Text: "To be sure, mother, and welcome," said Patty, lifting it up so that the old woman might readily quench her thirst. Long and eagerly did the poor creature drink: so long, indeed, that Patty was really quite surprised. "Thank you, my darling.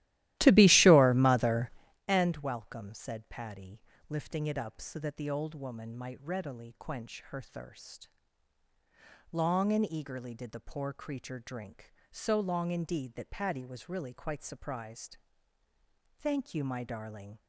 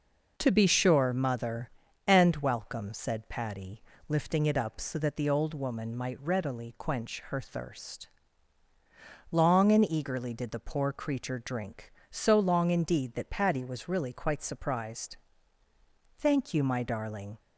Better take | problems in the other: second | starts louder than the rest; strong; until 2.0 s; 15.5 dB

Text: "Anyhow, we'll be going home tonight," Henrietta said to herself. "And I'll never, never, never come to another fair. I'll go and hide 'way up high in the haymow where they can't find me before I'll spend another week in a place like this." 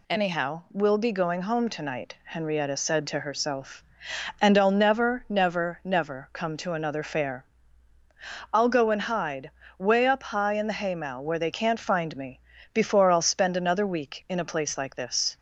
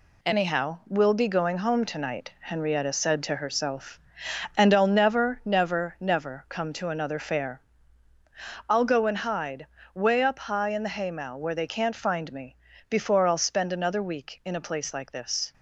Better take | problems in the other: first | gets quieter; noticeable; throughout; 6 dB // pauses between "hide" and "way"; slight; at 9.6 s; 0.30 s long; slight in the first // pauses between "me" and "before"; slight; at 12.5 s; 0.36 s long; slight in the first

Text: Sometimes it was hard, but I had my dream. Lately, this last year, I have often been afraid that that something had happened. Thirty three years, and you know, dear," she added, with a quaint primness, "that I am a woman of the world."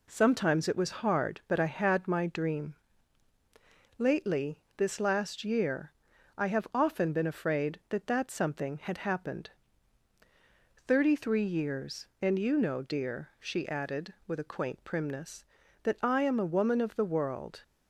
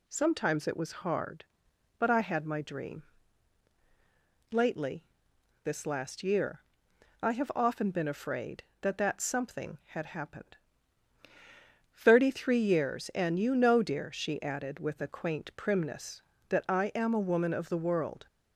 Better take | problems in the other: neither | none

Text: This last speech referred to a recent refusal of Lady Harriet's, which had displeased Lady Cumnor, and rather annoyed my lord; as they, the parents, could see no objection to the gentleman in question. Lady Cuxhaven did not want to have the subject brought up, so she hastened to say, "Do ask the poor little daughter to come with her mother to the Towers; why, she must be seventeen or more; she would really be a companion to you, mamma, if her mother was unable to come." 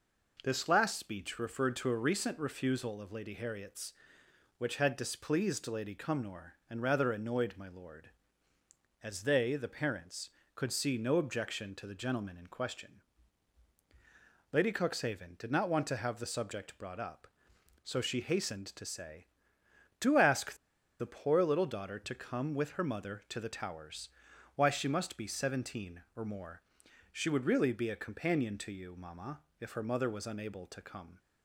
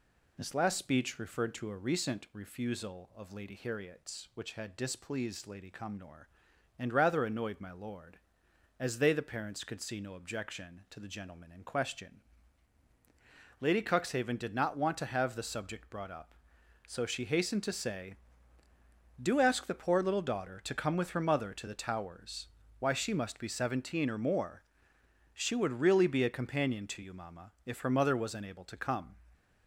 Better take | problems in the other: second | pauses between "ask" and "the"; at 20.5 s; 0.45 s long

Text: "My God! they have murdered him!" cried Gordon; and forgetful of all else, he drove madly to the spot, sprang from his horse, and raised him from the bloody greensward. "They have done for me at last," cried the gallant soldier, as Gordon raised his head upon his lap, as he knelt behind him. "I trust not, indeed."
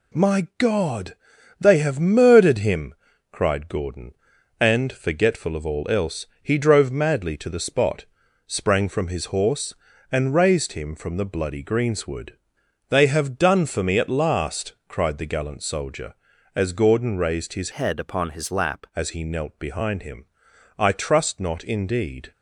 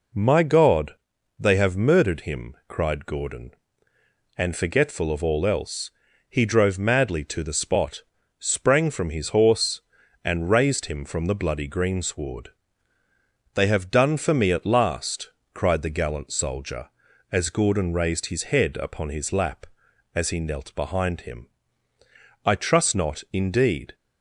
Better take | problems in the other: second | changes voice from "head" to "lap"; from 17.7 to 18.8 s; 1.1 s long

